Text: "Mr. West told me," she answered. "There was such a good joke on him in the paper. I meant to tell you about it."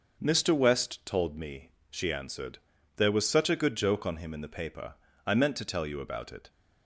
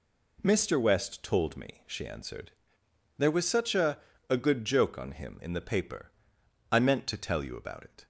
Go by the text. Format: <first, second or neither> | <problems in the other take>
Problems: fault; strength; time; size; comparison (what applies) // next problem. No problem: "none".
first | says "a" twice; at 4.2 s